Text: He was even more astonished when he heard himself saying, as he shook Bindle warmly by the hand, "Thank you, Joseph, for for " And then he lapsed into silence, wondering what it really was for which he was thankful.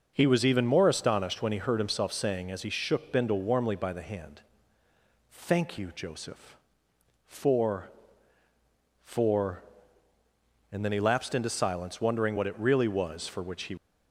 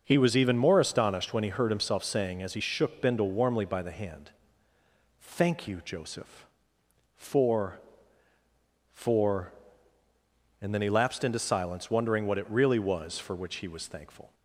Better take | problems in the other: second | starts louder than the rest; until 1.1 s; 6.5 dB; also in the second // stops before "was thankful"; at 13.7 s

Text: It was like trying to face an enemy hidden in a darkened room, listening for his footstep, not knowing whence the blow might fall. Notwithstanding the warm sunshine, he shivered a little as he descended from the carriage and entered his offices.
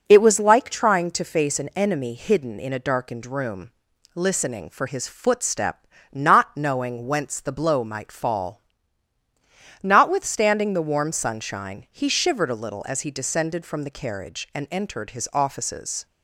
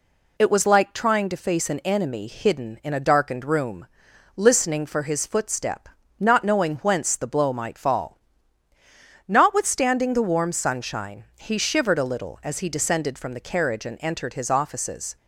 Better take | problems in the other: neither | none

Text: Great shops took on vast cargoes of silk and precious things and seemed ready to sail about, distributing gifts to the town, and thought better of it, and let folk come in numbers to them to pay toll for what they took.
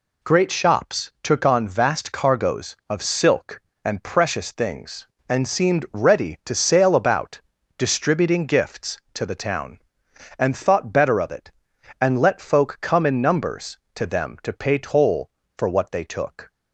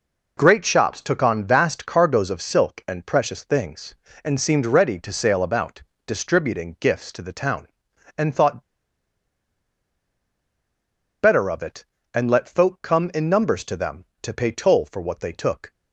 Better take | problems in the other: first | pauses between "thought" and "better"; strong; at 8.6 s; 2.6 s long

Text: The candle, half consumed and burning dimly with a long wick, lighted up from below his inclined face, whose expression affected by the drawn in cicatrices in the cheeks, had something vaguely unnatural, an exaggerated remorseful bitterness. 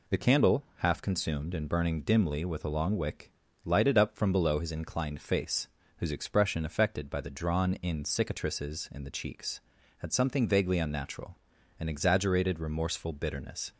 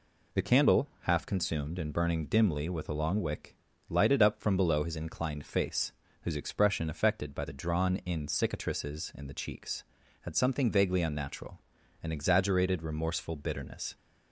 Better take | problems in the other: neither | none

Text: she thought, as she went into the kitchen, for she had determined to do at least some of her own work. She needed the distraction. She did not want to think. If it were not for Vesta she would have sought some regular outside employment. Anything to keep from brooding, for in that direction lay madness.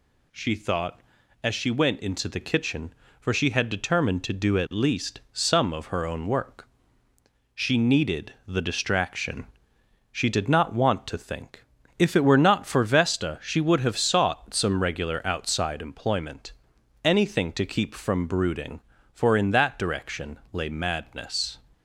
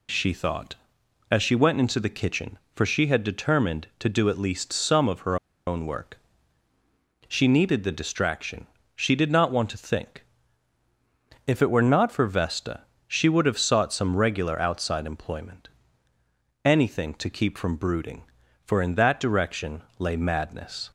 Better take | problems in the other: first | pauses between "her" and "own"; slight; at 5.3 s; 0.31 s long // pauses between "Vesta" and "she"; slight; at 12.8 s; 0.28 s long // pauses between "direction" and "lay"; slight; at 19.8 s; 0.18 s long

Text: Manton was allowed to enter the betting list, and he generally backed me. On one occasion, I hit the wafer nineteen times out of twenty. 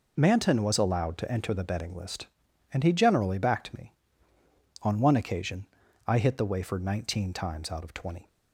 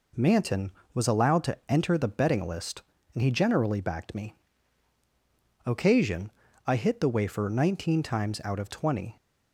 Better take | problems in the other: first | skips "On one"; at 5.0 s

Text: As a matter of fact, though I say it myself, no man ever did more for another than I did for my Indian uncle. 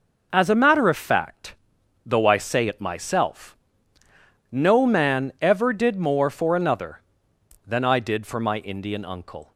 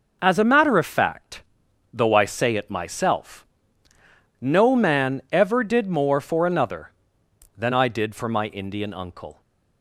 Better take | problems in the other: neither | none

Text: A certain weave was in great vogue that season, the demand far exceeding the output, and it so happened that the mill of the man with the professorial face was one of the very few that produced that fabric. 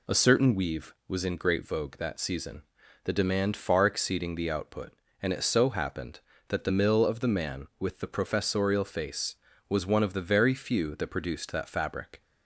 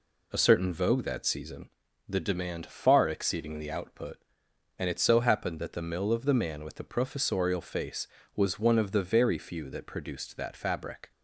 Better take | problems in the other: first | skips "weave was in great"; at 0.7 s

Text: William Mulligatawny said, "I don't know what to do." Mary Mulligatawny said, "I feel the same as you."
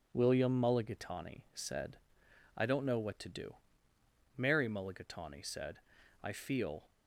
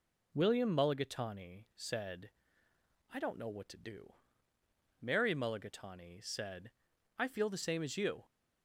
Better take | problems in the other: second | stops before "the same as you"; at 6.8 s

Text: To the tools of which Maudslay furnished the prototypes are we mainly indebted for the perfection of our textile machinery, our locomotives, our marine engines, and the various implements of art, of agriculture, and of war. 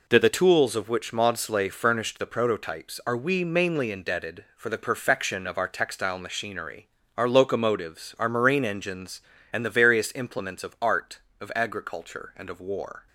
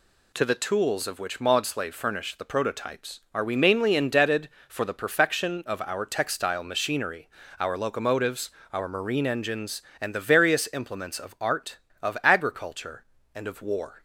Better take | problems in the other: neither | none

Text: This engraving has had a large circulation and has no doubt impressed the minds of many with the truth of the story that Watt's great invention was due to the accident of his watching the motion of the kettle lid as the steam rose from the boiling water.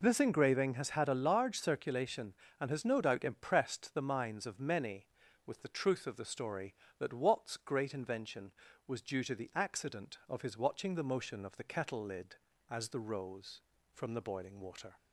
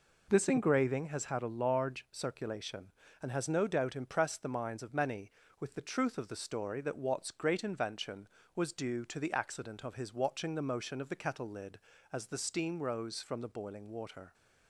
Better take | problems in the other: second | skips "steam"; at 12.9 s

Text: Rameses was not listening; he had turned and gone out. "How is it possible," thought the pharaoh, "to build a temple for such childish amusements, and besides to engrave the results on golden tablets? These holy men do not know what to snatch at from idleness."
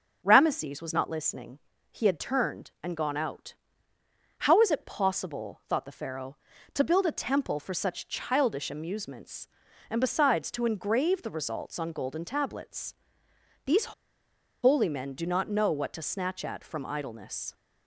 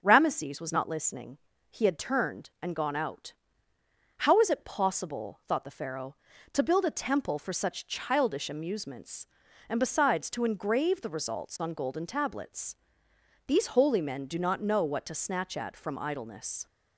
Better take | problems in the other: second | pauses between "These" and "holy"; noticeable; at 13.9 s; 0.69 s long

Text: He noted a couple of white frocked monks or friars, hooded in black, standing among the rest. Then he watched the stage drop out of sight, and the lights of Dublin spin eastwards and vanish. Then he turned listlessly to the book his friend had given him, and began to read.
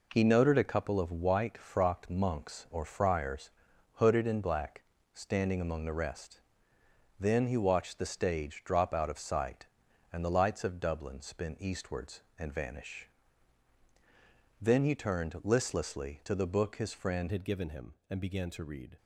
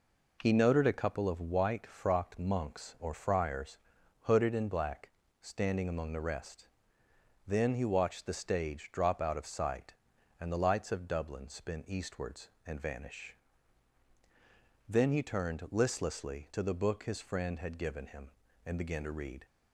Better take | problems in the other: second | changes voice at "had"; from 17.2 s on; 1.7 s long

